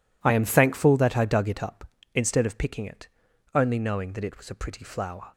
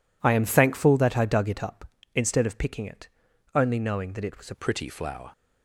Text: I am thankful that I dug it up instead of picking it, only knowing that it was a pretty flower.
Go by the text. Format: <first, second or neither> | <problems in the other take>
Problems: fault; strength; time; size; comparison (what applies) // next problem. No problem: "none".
first | changes voice at "pretty"; from 4.5 s on; 0.8 s long